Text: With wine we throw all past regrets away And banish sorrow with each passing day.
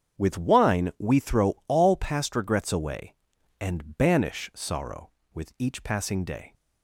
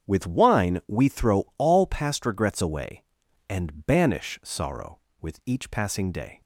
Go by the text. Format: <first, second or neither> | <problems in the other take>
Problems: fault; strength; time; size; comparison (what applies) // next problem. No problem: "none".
neither | starts louder than the rest; strong; the same in both